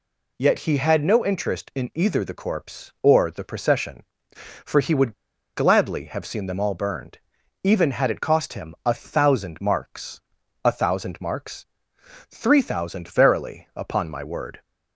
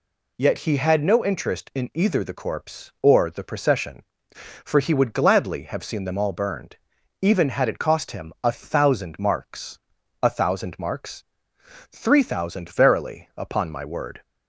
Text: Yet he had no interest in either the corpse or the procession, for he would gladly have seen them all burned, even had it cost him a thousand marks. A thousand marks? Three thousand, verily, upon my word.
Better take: second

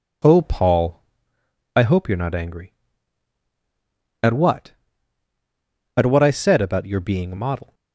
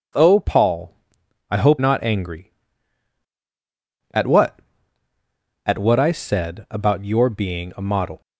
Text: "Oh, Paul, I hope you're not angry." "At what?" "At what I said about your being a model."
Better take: first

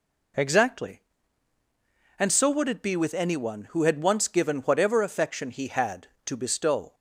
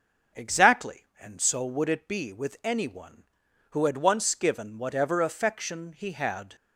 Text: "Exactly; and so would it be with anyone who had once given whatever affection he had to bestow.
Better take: first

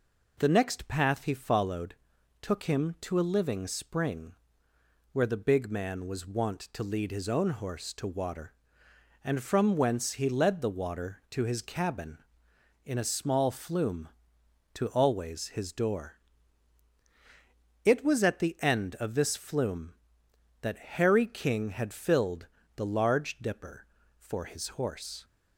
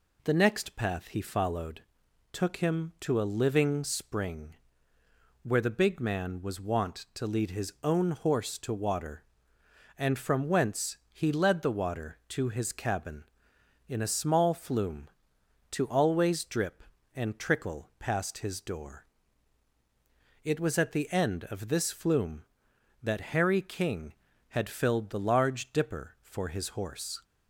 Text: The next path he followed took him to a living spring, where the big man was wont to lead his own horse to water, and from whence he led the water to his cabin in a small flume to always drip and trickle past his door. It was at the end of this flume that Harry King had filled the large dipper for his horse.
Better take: second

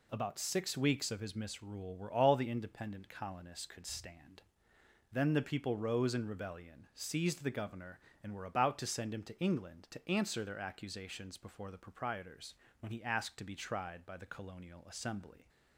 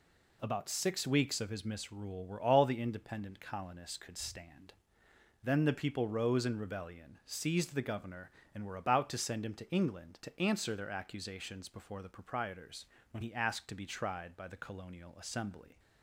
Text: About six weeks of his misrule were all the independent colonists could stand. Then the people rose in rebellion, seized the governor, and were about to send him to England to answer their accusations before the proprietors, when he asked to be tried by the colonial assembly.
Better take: neither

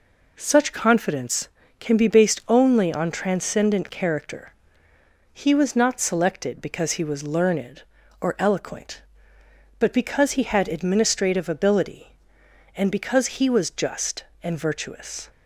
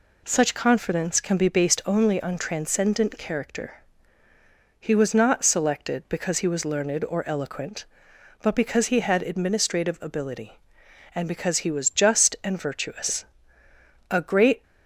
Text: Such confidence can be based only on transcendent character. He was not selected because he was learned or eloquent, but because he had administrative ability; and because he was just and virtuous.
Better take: first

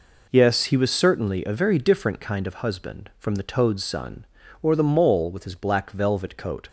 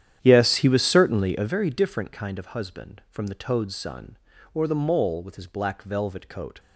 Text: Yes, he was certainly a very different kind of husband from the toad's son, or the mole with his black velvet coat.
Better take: first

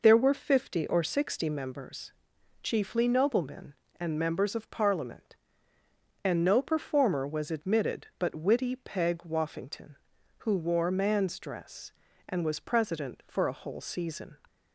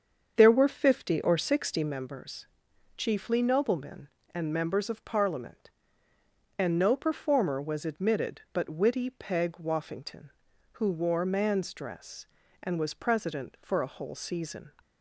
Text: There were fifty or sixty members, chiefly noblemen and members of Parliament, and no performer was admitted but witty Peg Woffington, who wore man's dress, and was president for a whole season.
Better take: first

